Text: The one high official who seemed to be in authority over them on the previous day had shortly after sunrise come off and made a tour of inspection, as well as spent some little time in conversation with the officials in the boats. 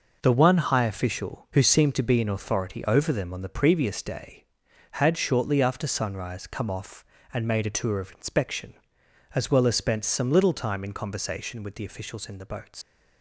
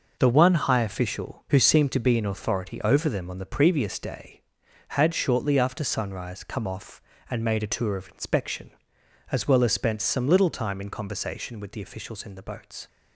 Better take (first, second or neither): second